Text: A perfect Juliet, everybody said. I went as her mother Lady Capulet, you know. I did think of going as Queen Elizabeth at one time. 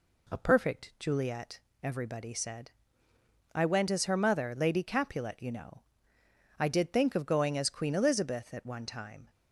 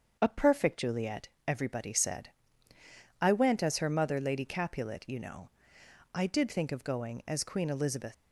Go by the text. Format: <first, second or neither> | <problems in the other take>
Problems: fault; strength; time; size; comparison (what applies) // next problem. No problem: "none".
first | starts louder than the rest; until 1.2 s; 7 dB // stops before "at one time"; at 8.1 s